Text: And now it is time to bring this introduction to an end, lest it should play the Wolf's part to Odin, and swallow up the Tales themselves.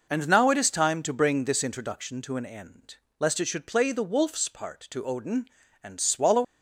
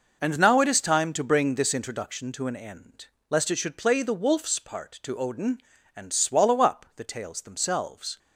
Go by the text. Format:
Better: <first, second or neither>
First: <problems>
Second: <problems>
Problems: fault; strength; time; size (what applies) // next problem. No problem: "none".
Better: second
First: stops before "up the Tales themselves"; at 6.4 s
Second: none